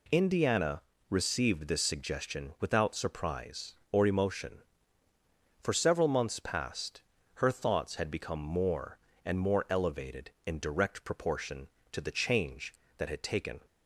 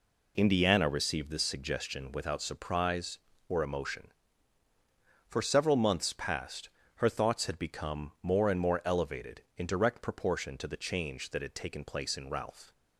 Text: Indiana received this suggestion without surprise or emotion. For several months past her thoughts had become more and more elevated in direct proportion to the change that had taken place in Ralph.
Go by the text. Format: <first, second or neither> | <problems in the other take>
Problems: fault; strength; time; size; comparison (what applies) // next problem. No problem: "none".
second | pauses between "Indiana" and "received"; slight; at 0.8 s; 0.28 s long // pauses between "past" and "her"; slight; at 7.0 s; 0.34 s long; slight in the second // stops before "place in Ralph"; at 13.6 s